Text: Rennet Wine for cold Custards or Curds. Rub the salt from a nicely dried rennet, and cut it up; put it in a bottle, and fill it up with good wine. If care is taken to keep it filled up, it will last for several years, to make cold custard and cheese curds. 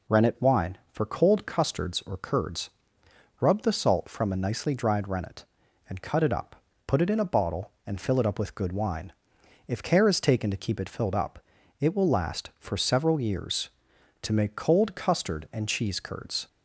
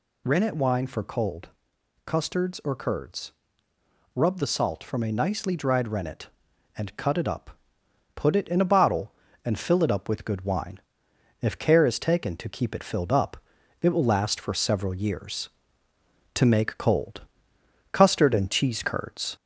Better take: first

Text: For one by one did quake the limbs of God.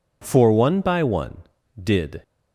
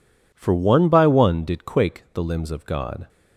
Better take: second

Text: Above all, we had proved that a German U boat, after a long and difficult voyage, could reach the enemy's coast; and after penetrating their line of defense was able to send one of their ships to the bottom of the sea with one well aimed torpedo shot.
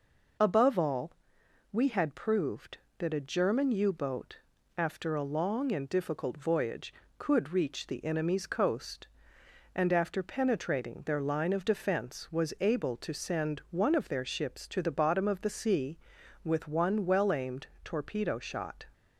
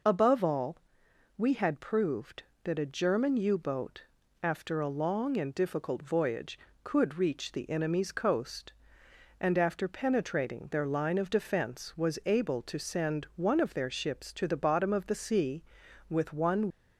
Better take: first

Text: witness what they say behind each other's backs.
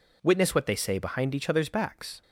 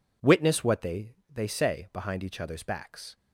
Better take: first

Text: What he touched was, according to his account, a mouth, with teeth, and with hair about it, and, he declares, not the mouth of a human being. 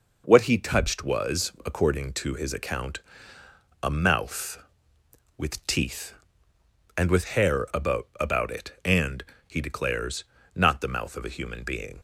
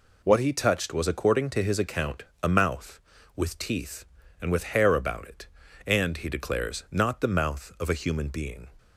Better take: second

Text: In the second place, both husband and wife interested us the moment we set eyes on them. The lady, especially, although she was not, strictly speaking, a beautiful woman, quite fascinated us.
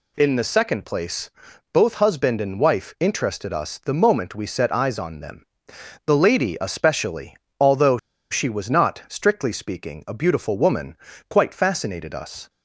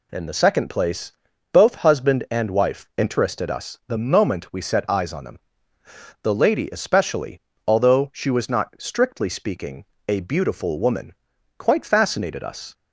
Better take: second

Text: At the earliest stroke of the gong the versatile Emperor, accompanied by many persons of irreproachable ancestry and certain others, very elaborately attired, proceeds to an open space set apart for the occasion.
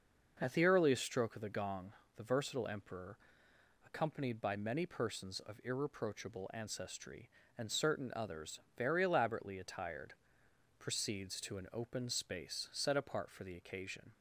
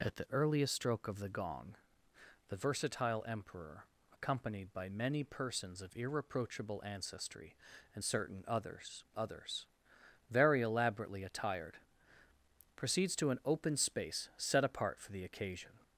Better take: first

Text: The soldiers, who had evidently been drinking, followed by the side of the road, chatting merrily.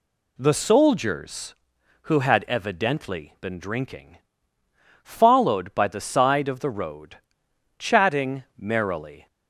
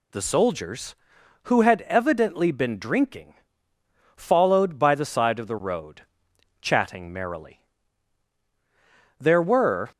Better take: first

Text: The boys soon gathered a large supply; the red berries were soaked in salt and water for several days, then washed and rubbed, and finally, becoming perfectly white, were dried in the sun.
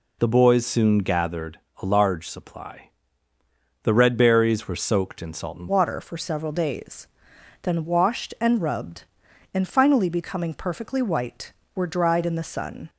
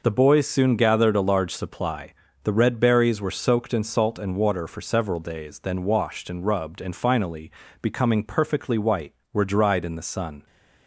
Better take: second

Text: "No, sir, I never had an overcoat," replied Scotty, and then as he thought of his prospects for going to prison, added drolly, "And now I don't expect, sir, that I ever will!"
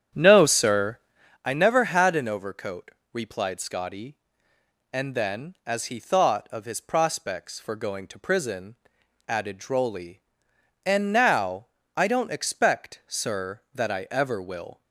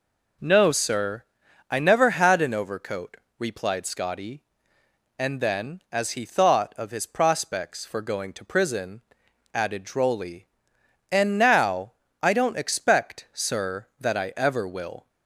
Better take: second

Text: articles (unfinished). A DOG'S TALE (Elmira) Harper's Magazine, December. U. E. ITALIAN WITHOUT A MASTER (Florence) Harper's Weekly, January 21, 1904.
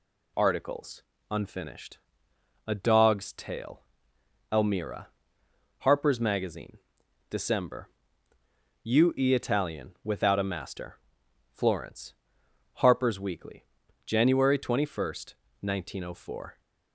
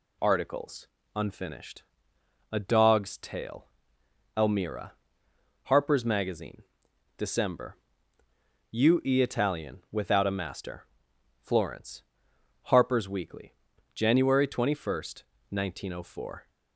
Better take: neither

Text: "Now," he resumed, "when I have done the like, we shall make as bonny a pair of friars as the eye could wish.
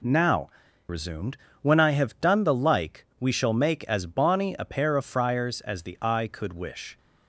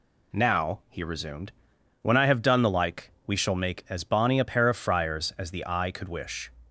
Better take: second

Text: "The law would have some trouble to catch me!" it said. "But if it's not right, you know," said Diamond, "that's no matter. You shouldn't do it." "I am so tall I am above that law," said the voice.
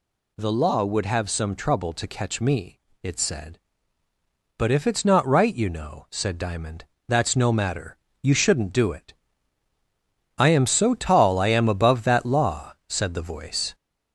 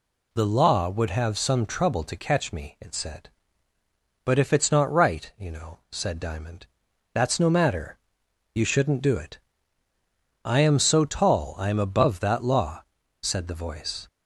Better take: second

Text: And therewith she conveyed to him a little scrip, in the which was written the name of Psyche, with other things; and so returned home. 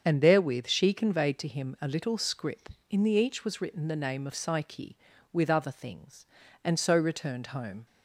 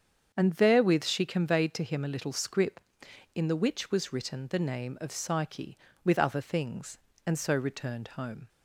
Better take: second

